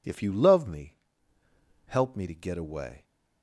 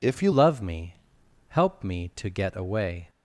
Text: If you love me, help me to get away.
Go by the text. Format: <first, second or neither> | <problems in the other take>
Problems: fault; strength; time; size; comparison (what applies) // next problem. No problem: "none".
first | changes voice at "love"; from 0.3 s on; 2.7 s long